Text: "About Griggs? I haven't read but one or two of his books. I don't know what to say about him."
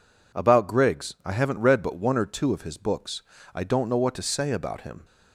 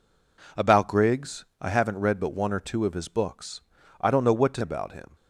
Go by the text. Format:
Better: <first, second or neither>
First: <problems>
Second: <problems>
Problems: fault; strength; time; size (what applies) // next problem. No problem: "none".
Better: first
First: none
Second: skips "say"; at 4.6 s